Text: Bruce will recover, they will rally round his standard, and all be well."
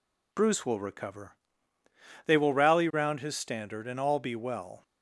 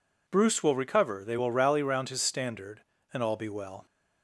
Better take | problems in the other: neither | none

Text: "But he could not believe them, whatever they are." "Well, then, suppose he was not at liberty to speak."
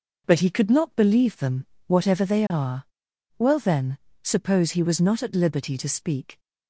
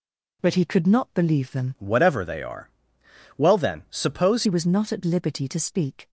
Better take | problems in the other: first | changes voice from "whatever" to "suppose"; from 1.7 to 4.4 s; 2.7 s long

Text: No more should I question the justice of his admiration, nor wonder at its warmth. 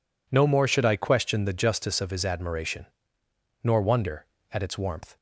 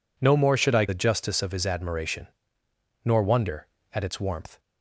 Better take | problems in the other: first | skips "question"; at 0.8 s

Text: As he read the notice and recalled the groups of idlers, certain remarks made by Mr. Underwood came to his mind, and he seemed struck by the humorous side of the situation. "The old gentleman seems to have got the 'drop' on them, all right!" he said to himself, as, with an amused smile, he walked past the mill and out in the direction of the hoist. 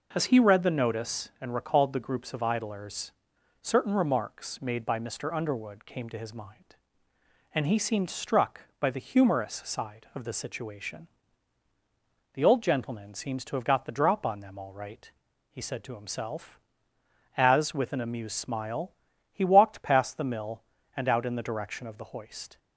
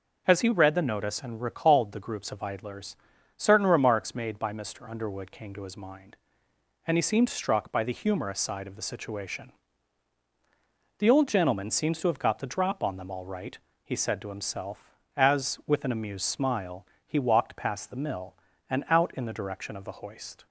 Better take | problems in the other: neither | none

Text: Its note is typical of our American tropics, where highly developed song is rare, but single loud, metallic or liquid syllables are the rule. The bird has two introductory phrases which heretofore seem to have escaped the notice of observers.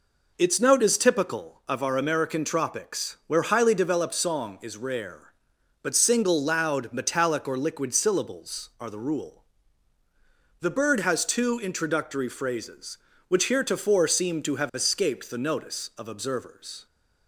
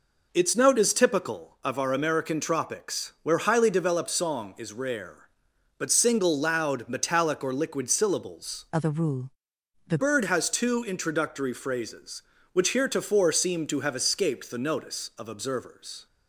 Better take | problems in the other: first | changes voice from "are" to "The"; from 8.7 to 9.9 s; 1.2 s long

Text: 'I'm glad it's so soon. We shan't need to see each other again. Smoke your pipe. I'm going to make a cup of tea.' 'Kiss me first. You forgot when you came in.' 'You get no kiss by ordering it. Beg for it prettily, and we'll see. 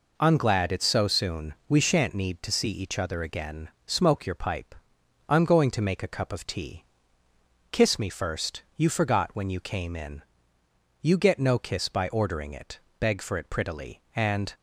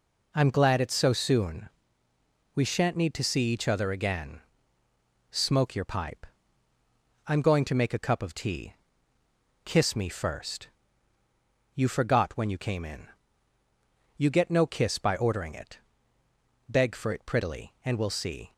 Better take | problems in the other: second | stops before "we'll see"; at 14.5 s

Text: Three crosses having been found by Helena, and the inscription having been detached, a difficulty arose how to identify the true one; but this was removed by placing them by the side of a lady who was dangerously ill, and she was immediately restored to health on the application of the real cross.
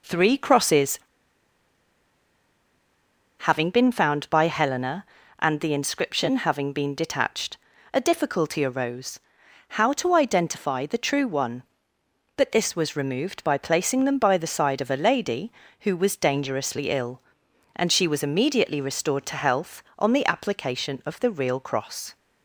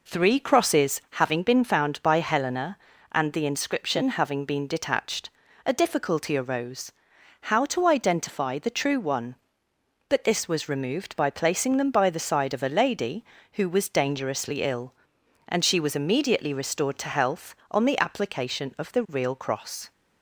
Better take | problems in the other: second | pauses between "crosses" and "having"; strong; at 0.9 s; 2.4 s long // pauses between "arose" and "how"; noticeable; at 9.2 s; 0.48 s long; noticeable in the second

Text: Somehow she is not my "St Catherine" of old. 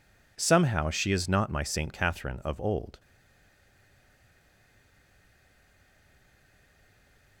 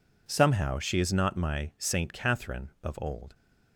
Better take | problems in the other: second | stays silent after the last word; strong; from 2.9 s on; 4.5 s long

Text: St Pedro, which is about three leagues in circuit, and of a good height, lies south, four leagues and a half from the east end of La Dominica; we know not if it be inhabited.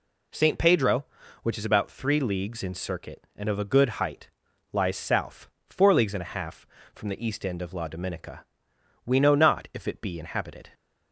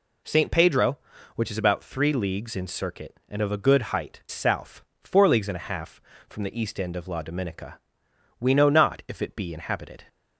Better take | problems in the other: first | skips "lies"; at 4.2 s

